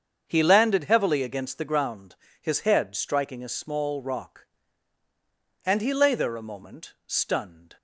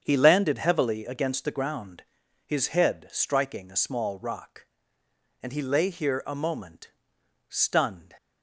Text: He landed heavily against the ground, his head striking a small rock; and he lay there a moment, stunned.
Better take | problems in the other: first | starts louder than the rest; strong; until 1.0 s; 7.5 dB; strong in the first // says "here" for "there"; at 5.8 s

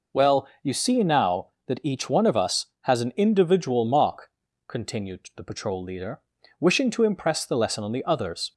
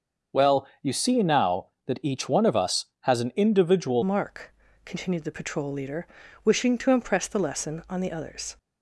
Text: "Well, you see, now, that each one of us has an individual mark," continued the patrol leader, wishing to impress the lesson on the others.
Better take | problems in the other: first | starts louder than the rest; until 1.4 s; 6.5 dB // changes voice at "mark"; from 4.0 s on; 4.5 s long

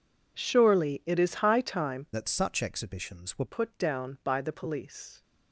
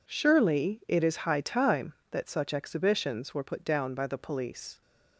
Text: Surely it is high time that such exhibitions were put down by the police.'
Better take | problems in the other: second | changes voice from "that" to "were"; from 2.1 to 3.4 s; 1.3 s long

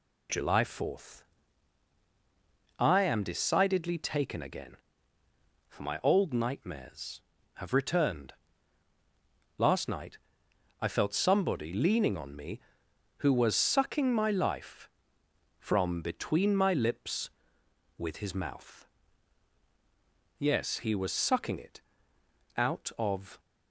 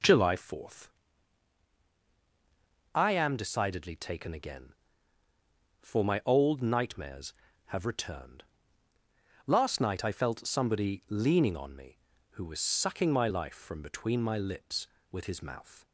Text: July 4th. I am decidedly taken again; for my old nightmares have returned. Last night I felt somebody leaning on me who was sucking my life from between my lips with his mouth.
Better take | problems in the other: second | pauses between "night" and "I"; noticeable; at 10.1 s; 0.62 s long // goes on to say "Yes he was sucking it out of"; strong; from 20.3 s on; 3.0 s long

